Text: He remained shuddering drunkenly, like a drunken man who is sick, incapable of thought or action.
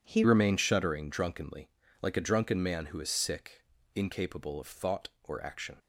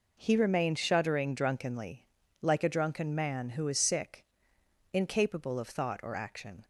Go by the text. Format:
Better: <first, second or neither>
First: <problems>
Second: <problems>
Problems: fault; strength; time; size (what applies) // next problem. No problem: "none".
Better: second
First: changes voice at "remained"; from 0.2 s on; 5.5 s long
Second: none